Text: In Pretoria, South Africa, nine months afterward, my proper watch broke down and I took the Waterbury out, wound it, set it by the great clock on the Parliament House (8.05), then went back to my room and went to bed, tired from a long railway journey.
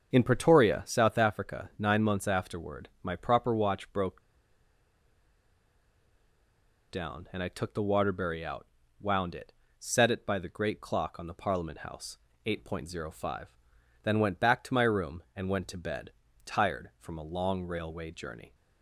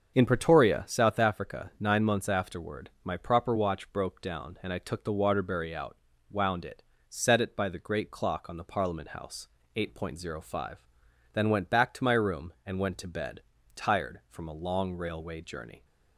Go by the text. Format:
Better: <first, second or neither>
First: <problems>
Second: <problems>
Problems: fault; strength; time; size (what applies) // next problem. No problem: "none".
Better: second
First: starts louder than the rest; until 1.1 s; 7 dB // pauses between "broke" and "down"; strong; at 4.2 s; 2.6 s long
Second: starts louder than the rest; until 1.1 s; 7 dB